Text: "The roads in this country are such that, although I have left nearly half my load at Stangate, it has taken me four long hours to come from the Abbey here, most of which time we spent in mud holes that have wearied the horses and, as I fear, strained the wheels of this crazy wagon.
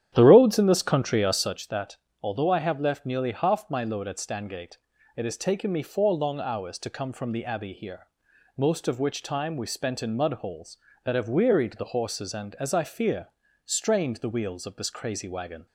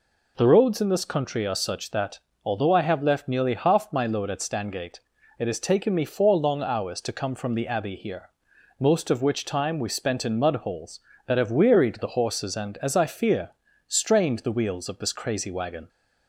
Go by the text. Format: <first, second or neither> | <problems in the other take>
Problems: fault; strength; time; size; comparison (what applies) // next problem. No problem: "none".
second | starts louder than the rest; strong; until 1.6 s; 10.5 dB